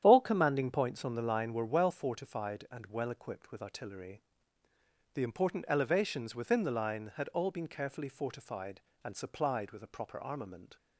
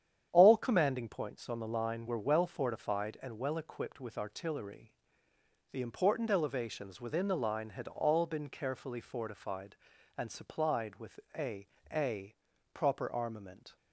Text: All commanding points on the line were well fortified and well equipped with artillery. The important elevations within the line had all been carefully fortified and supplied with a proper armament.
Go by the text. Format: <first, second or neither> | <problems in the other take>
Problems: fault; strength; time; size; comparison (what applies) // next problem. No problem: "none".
first | starts louder than the rest; strong; until 1.3 s; 9 dB; strong in the first // pauses between "with" and "a"; slight; at 11.2 s; 0.18 s long // says "a" twice; at 11.9 s